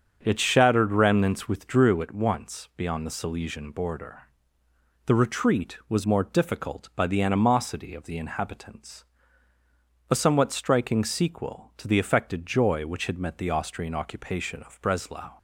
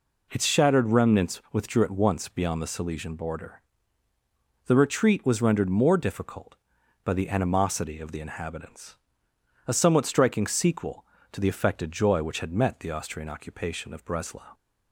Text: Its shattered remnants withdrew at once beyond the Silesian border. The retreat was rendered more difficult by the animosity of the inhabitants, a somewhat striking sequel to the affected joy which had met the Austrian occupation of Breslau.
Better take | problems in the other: second | starts louder than the rest; until 1.2 s; 7 dB // skips "rendered"; at 6.0 s

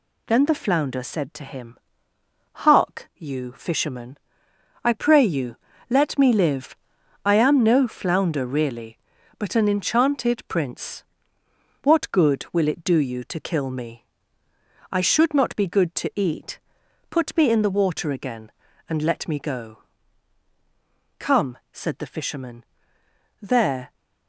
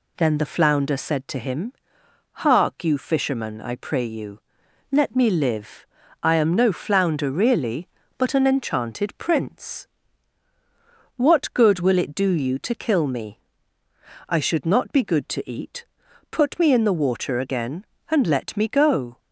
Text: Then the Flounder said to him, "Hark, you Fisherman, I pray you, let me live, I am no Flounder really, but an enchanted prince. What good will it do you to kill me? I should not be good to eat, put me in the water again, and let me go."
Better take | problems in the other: second | goes on to say "Come said the Fisherman there"; strong; from 21.1 s on; 2.7 s long

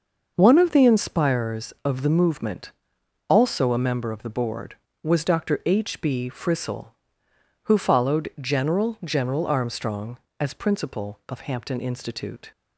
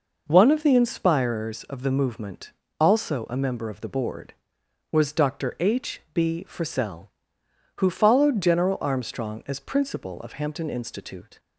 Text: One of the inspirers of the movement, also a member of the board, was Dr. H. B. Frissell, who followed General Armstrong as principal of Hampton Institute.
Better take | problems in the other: second | starts louder than the rest; noticeable; until 1.3 s; 6 dB // says "General" twice; at 9.0 s

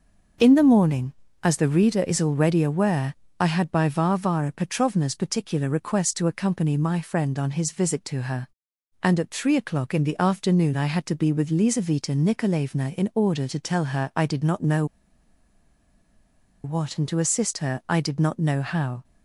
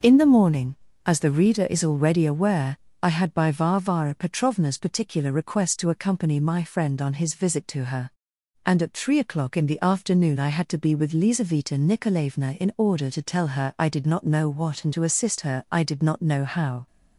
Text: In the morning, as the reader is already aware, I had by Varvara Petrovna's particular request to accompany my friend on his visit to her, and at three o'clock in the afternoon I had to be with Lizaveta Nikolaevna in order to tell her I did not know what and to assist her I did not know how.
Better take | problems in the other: second | starts louder than the rest; noticeable; until 1.7 s; 6 dB // pauses between "know" and "what"; strong; at 14.8 s; 1.7 s long

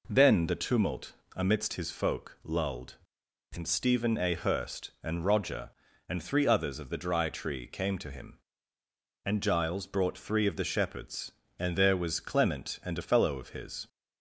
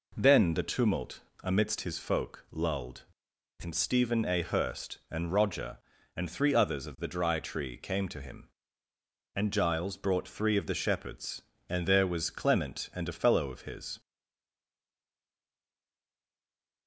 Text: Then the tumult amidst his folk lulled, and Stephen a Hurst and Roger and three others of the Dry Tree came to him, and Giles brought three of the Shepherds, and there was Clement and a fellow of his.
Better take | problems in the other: first | pauses between "tumult" and "amidst"; slight; at 1.2 s; 0.20 s long; slight in the first // stays silent after the last word; strong; from 14.0 s on; 2.8 s long

